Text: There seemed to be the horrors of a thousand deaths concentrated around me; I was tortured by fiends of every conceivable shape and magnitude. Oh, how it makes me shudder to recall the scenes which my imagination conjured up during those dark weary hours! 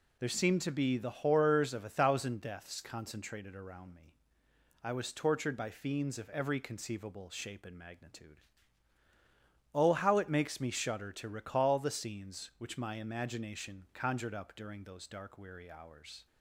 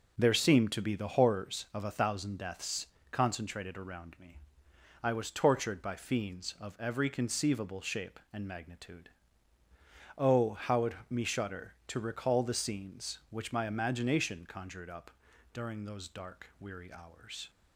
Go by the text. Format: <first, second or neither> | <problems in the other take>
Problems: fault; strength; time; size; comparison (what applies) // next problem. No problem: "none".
first | pauses between "deaths" and "concentrated"; slight; at 2.8 s; 0.26 s long // skips "makes"; at 11.0 s // pauses between "up" and "during"; at 15.0 s; 0.42 s long